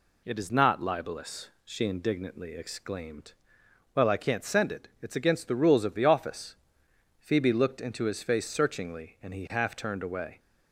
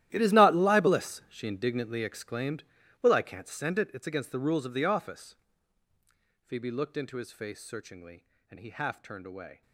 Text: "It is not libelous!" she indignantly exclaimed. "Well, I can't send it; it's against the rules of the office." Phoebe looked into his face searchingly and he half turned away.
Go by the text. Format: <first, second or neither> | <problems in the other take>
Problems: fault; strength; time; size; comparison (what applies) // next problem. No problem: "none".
first | gets quieter; strong; throughout; 17 dB